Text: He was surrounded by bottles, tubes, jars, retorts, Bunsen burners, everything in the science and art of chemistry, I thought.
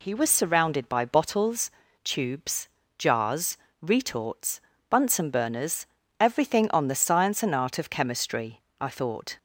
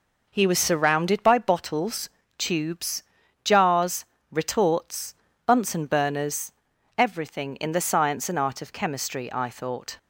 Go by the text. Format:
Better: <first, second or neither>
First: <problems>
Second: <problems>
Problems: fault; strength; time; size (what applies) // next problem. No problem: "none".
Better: second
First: says "on" for "in"; at 6.7 s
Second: none